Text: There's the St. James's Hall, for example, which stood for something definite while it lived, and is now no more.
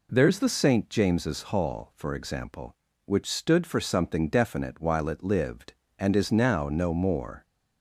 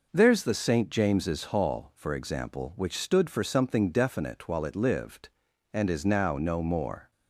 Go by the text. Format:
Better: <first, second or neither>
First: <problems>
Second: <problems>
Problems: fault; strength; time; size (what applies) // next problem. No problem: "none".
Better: neither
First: none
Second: none